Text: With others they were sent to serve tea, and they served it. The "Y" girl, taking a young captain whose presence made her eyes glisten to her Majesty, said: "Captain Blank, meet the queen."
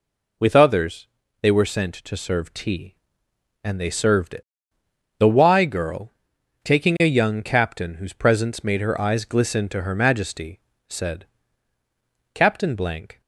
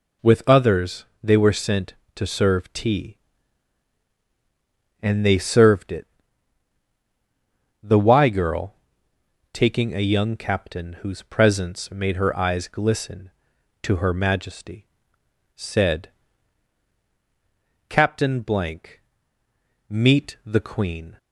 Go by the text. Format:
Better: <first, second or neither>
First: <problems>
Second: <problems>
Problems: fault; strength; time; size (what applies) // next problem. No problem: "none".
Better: second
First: pauses between "others" and "they"; slight; at 1.0 s; 0.34 s long // stops before "meet the queen"; at 13.2 s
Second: pauses between "others" and "they"; slight; at 1.0 s; 0.18 s long